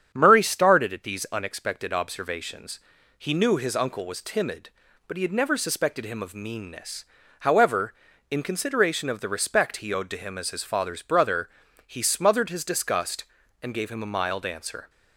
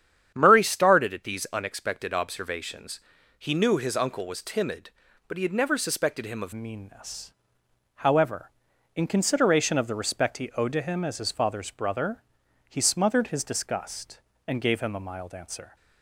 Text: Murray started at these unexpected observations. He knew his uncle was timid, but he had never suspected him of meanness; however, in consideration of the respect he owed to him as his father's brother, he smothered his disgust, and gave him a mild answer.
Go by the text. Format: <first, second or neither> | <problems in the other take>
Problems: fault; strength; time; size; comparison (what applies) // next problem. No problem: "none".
first | starts louder than the rest; strong; until 1.3 s; 9 dB; strong in the first // changes voice at "meanness"; from 6.5 s on; 9.2 s long